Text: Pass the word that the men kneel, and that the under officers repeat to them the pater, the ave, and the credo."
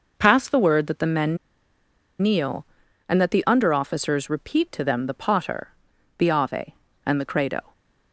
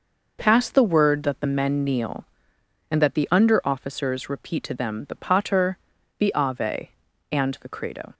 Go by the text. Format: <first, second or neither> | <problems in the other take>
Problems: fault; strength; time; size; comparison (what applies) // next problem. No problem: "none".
second | pauses between "men" and "kneel"; noticeable; at 1.3 s; 0.85 s long